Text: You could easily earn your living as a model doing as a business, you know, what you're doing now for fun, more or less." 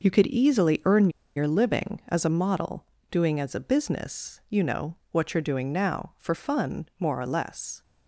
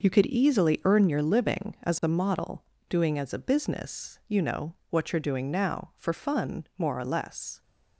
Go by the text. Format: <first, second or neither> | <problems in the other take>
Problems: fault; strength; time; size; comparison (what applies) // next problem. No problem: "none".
second | pauses between "earn" and "your"; slight; at 1.0 s; 0.26 s long // pauses between "model" and "doing"; slight; at 2.8 s; 0.26 s long; slight in the second